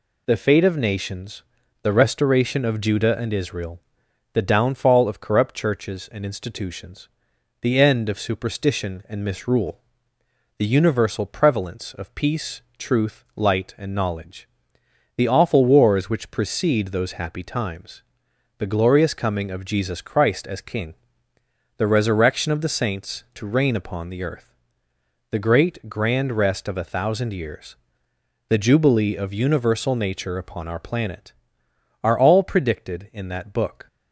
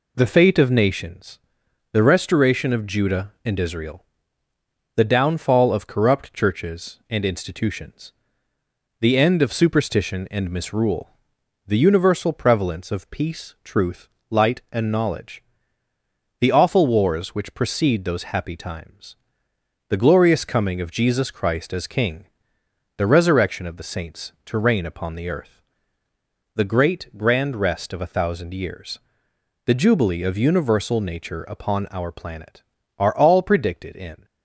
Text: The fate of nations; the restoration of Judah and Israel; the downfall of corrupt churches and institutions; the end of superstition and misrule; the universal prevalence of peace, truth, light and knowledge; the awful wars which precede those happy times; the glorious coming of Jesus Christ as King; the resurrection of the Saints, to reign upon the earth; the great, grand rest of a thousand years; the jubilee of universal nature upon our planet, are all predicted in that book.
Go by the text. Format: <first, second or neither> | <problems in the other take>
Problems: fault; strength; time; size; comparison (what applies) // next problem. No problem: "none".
first | stops before "that book"; at 34.2 s